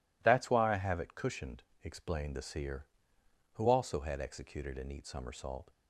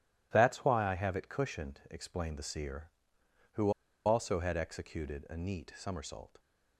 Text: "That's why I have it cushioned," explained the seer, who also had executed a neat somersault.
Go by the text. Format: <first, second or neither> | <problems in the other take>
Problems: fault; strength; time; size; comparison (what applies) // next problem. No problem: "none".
first | pauses between "who" and "also"; slight; at 3.6 s; 0.35 s long